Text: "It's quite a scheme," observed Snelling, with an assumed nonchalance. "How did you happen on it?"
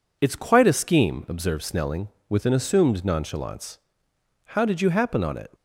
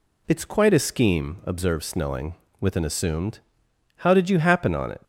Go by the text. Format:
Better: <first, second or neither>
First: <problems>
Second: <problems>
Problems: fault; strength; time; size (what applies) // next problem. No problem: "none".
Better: first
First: none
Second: skips "nonchalance"; at 3.6 s